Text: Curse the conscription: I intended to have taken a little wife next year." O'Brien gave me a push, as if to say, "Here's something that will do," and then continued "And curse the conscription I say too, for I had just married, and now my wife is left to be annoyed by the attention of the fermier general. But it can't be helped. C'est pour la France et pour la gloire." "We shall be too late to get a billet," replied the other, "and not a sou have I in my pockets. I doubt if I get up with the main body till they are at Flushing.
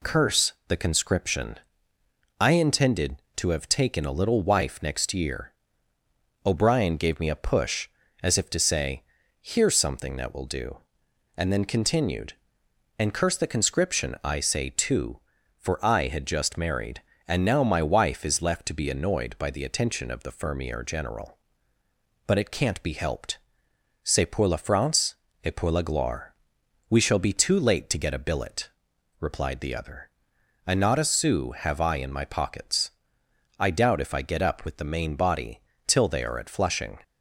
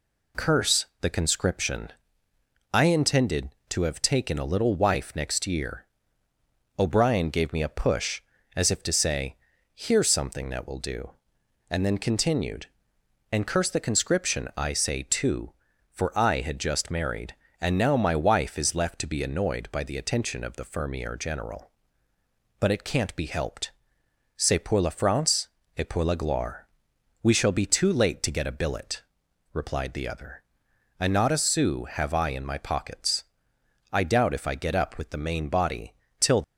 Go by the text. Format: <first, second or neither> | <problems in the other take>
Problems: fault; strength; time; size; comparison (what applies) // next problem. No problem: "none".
first | pauses between "Curse" and "the"; slight; at 0.8 s; 0.16 s long; slight in the first // pauses between "France" and "et"; slight; at 25.4 s; 0.30 s long; slight in the first // pauses between "body" and "till"; slight; at 35.9 s; 0.26 s long; slight in the first // stops before "they are at Flushing"; at 36.4 s